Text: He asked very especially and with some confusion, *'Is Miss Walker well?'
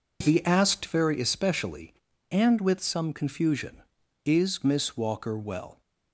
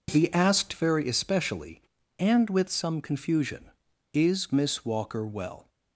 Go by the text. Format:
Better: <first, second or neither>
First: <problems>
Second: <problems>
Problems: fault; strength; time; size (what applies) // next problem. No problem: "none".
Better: neither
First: none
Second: none